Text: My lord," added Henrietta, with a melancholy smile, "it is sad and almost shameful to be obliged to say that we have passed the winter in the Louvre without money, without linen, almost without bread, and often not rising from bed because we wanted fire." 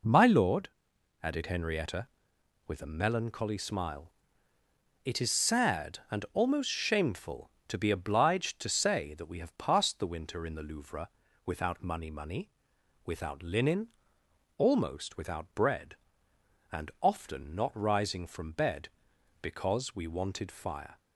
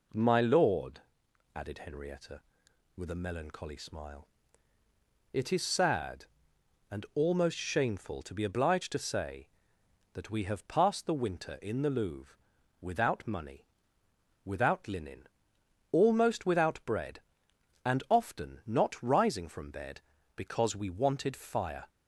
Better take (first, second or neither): second